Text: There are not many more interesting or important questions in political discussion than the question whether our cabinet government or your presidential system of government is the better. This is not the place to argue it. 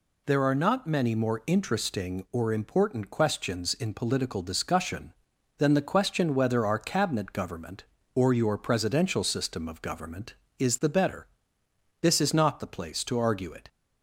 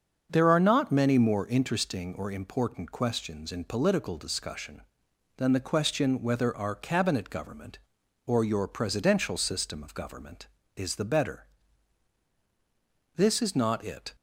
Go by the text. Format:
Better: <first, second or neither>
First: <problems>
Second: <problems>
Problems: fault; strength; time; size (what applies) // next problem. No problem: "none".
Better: first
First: none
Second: starts louder than the rest; until 1.3 s; 7 dB // skips "the place to argue"; at 13.8 s